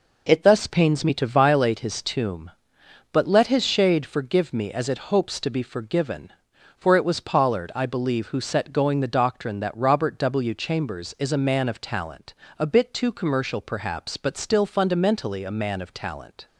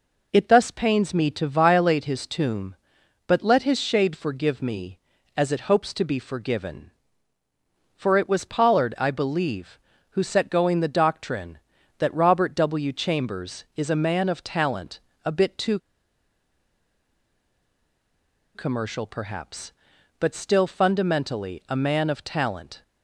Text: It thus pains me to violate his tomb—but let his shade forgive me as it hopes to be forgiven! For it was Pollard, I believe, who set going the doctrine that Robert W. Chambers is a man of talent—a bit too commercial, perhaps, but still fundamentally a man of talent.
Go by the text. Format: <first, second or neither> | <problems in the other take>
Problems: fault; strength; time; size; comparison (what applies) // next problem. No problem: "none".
first | pauses between "too" and "commercial"; strong; at 15.7 s; 2.7 s long